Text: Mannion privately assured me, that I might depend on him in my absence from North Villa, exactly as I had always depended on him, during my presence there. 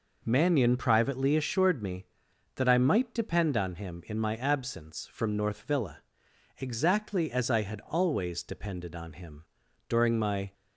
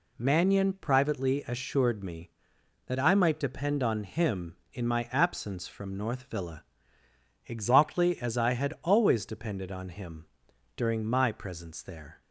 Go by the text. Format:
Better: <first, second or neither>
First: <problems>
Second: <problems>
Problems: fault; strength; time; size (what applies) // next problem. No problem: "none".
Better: second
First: stops before "presence there"; at 10.5 s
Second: none